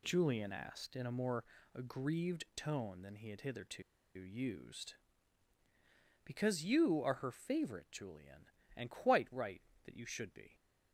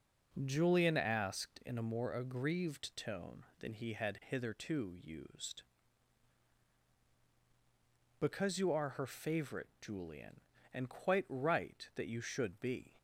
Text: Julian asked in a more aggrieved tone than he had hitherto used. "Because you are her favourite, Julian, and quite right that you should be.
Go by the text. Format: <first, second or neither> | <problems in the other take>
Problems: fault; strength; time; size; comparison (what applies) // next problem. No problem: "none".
second | pauses between "more" and "aggrieved"; slight; at 1.4 s; 0.30 s long // pauses between "hitherto" and "used"; slight; at 3.8 s; 0.33 s long